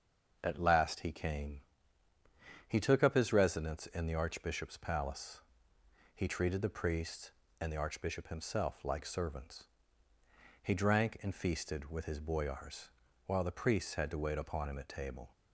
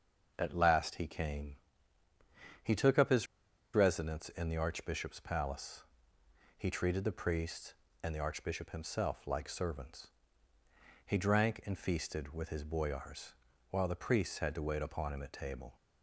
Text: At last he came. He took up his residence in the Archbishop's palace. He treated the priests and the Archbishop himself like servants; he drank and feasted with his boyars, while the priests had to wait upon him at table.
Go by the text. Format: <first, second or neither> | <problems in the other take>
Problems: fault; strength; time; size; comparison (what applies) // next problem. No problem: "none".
first | starts louder than the rest; until 1.3 s; 6.5 dB; also in the first // pauses between "his" and "residence"; noticeable; at 3.2 s; 0.49 s long